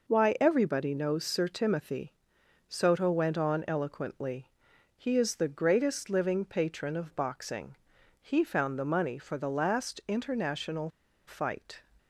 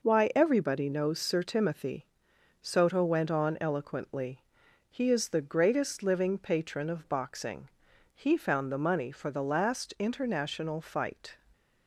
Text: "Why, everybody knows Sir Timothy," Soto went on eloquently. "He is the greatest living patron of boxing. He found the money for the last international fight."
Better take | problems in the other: second | pauses between "international" and "fight"; at 10.8 s; 0.39 s long

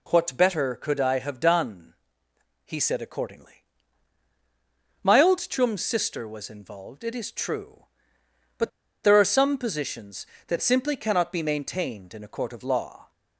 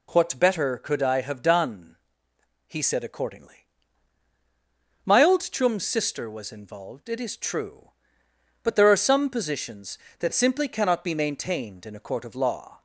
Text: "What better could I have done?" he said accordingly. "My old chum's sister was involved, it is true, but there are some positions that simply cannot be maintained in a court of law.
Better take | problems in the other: second | pauses between "but" and "there"; slight; at 8.6 s; 0.34 s long

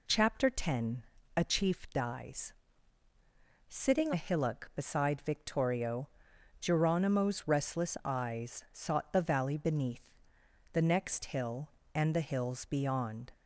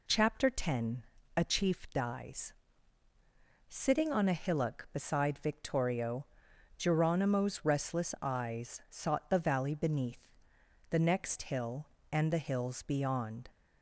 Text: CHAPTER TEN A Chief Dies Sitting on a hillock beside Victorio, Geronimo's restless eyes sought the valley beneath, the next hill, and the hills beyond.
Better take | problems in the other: second | pauses between "TEN" and "A"; slight; at 1.0 s; 0.34 s long; slight in the second // pauses between "Dies" and "Sitting"; at 2.5 s; 1.1 s long; also in the second // skips "on"; at 4.1 s

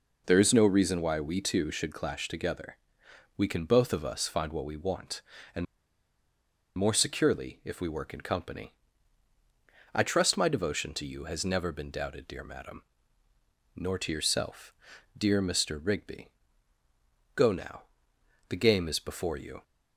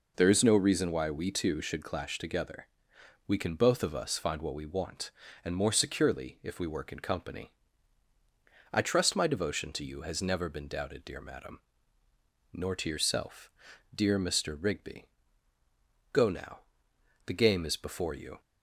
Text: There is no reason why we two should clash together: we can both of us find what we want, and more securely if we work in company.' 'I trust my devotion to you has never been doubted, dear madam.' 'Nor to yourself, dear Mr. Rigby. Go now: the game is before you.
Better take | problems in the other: second | pauses between "and" and "more"; at 5.6 s; 1.1 s long

